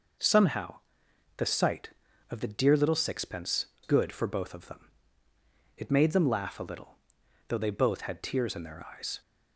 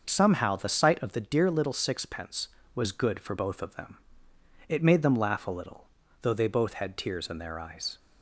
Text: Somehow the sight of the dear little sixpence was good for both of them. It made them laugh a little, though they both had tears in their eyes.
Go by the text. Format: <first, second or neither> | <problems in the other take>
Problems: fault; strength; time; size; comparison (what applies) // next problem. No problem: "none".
second | pauses between "Somehow" and "the"; noticeable; at 0.7 s; 0.58 s long // skips "was"; at 3.7 s